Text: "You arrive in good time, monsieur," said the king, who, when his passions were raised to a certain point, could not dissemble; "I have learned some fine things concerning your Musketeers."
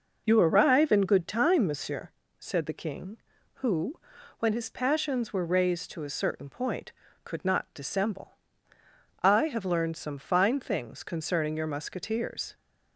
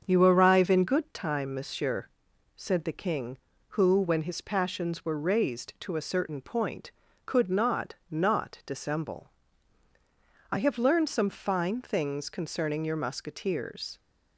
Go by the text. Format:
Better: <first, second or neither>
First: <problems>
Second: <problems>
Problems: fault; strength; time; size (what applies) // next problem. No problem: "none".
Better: first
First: none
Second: starts louder than the rest; strong; until 1.0 s; 7 dB // says "not" twice; at 8.1 s